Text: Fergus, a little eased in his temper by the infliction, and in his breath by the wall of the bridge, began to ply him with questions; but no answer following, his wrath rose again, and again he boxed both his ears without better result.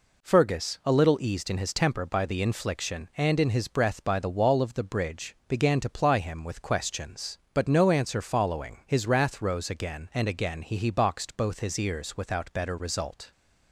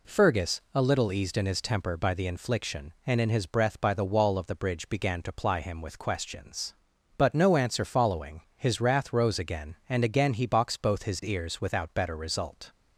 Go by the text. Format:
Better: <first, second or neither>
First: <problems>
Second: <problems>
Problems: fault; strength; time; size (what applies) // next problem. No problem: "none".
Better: second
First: says "he" twice; at 10.7 s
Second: none